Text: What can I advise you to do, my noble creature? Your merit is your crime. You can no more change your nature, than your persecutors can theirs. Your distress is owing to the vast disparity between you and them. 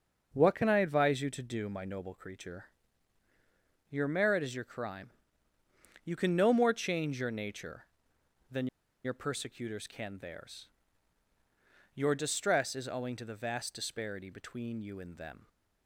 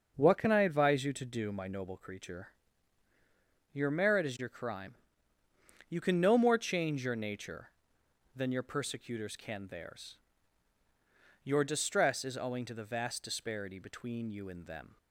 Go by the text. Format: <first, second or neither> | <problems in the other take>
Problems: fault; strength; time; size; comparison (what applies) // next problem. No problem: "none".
second | pauses between "than" and "your"; at 8.6 s; 0.38 s long